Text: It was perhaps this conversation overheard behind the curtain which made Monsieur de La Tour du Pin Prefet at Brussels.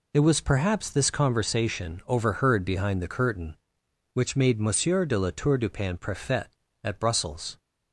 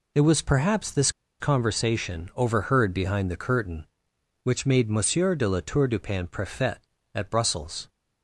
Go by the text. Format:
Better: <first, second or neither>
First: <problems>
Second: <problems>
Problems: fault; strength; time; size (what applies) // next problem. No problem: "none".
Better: first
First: none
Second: pauses between "this" and "conversation"; slight; at 1.1 s; 0.28 s long